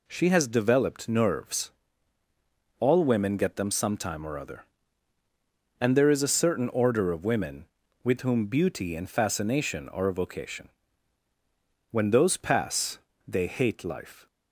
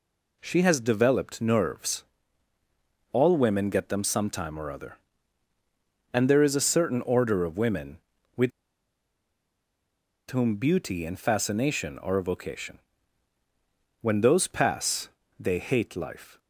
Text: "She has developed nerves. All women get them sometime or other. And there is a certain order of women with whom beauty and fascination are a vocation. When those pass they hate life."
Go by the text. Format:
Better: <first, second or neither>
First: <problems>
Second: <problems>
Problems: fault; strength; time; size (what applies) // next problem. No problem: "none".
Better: first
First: pauses between "pass" and "they"; slight; at 12.9 s; 0.28 s long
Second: pauses between "with" and "whom"; strong; at 8.5 s; 1.7 s long // pauses between "pass" and "they"; slight; at 15.0 s; 0.30 s long